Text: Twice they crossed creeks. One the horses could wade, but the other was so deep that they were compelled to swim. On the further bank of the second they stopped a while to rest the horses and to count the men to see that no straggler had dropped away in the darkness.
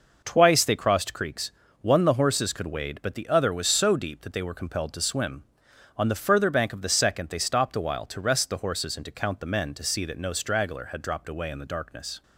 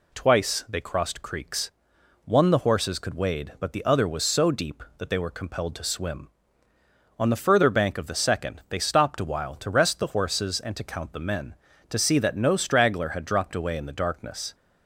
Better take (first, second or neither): neither